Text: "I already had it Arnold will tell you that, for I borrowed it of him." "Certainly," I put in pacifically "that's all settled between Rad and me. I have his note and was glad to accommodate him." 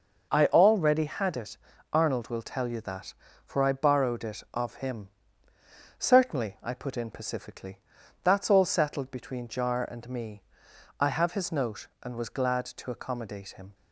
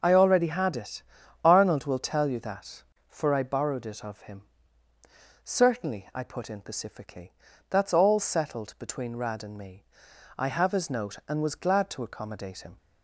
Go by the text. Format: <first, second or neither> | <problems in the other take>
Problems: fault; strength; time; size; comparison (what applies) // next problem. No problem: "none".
second | pauses between "it" and "Arnold"; slight; at 1.5 s; 0.36 s long; also in the second // pauses between "pacifically" and "that's"; noticeable; at 7.7 s; 0.46 s long; also in the second // says "Jar" for "Rad"; at 9.4 s